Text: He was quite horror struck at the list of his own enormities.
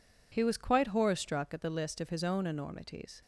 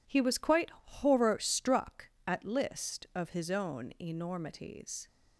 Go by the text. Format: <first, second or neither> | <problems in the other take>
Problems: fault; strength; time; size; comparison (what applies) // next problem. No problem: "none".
first | pauses between "quite" and "horror"; slight; at 0.6 s; 0.16 s long // skips "the"; at 2.4 s